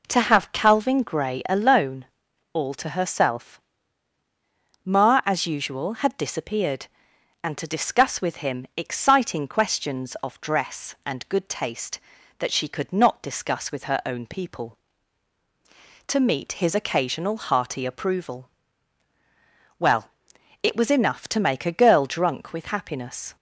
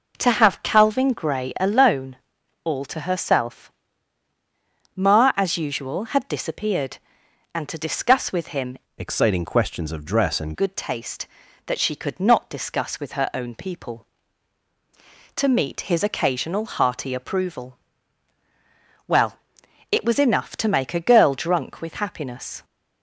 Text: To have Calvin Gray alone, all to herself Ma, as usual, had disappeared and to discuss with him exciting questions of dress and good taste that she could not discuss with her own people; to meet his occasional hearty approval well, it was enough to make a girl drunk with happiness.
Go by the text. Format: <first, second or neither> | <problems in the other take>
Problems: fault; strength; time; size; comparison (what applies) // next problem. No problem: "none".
first | pauses between "herself" and "Ma"; strong; at 3.6 s; 1.2 s long; strong in the first // changes voice from "exciting" to "and"; from 8.9 to 10.5 s; 1.6 s long // pauses between "approval" and "well"; strong; at 17.7 s; 1.3 s long; strong in the first